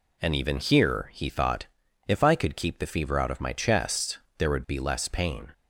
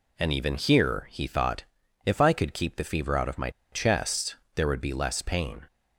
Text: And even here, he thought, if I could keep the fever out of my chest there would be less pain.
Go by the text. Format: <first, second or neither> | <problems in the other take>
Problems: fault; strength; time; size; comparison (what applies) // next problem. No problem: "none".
first | pauses between "my" and "chest"; slight; at 3.4 s; 0.22 s long // pauses between "chest" and "there"; slight; at 4.3 s; 0.20 s long; slight in the first